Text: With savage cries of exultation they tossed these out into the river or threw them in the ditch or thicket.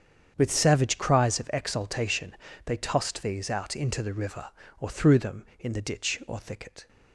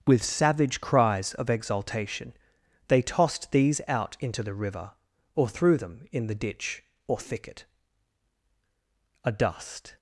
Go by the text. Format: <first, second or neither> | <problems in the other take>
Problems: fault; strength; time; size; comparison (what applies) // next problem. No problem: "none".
first | starts louder than the rest; strong; until 1.0 s; 7.5 dB; strong in the first // pauses between "exultation" and "they"; noticeable; at 2.3 s; 0.54 s long; slight in the first // goes on to say "A dust"; noticeable; from 9.2 s on; 0.74 s long